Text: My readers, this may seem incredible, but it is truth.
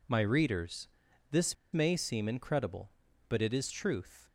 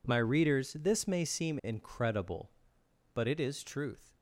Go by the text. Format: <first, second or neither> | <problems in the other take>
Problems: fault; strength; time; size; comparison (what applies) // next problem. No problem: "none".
second | pauses between "this" and "may"; slight; at 1.5 s; 0.17 s long